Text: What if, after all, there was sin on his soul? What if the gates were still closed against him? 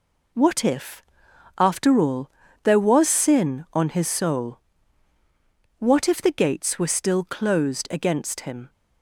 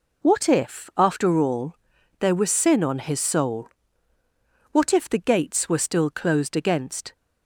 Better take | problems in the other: first | stops before "him"; at 7.1 s

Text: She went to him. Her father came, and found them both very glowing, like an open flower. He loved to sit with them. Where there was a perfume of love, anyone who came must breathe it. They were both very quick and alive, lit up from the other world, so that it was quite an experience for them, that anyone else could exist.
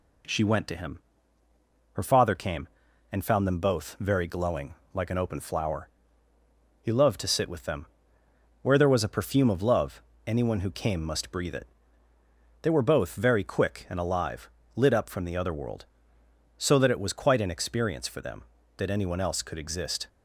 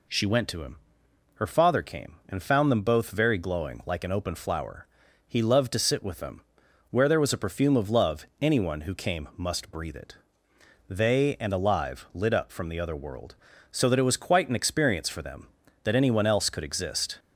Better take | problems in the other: first | skips "were both very quick"; at 11.3 s

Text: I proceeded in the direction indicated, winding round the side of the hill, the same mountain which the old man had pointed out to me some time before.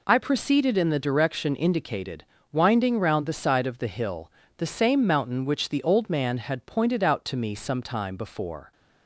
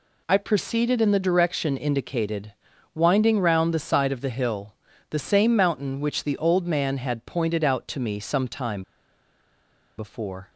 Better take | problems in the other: first | pauses between "time" and "before"; at 8.8 s; 1.1 s long

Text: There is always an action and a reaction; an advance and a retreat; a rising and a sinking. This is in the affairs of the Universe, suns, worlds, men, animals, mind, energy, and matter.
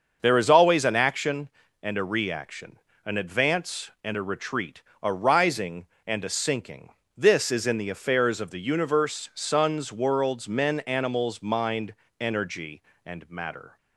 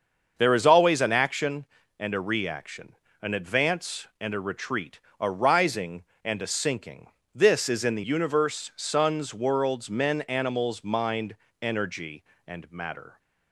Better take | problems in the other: first | starts louder than the rest; until 1.3 s; 6.5 dB; also in the first // skips "affairs of the"; at 8.0 s

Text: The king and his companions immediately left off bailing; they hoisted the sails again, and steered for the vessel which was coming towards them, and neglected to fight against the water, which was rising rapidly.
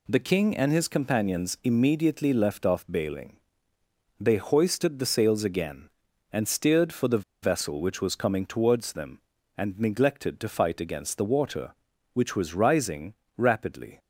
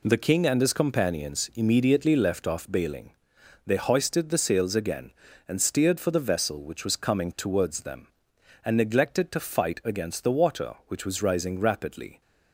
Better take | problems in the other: second | pauses between "the" and "vessel"; slight; at 7.2 s; 0.18 s long // pauses between "rising" and "rapidly"; slight; at 13.1 s; 0.22 s long

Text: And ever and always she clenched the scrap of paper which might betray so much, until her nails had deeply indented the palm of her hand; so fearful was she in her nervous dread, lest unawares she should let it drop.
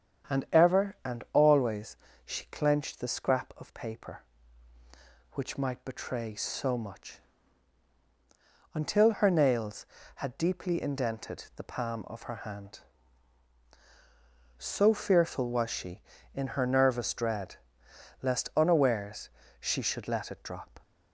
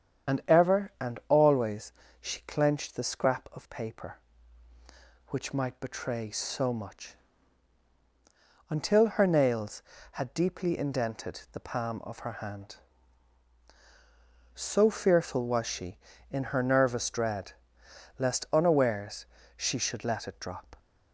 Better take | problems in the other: first | loses the start of "And"; at 0.2 s; 70 ms // starts louder than the rest; strong; until 1.5 s; 8 dB; strong in the first // pauses between "always" and "she"; slight; at 1.9 s; 0.28 s long; slight in the first // pauses between "unawares" and "she"; slight; at 19.2 s; 0.32 s long; slight in the first

